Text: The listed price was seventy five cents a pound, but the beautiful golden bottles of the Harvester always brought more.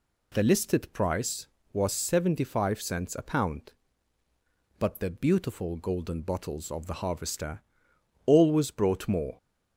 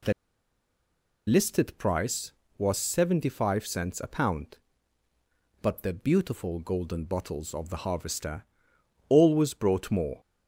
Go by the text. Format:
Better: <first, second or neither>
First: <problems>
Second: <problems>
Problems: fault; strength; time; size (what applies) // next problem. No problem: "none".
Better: first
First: pauses between "Harvester" and "always"; noticeable; at 7.6 s; 0.64 s long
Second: pauses between "The" and "listed"; at 0.1 s; 1.1 s long // pauses between "Harvester" and "always"; noticeable; at 8.4 s; 0.64 s long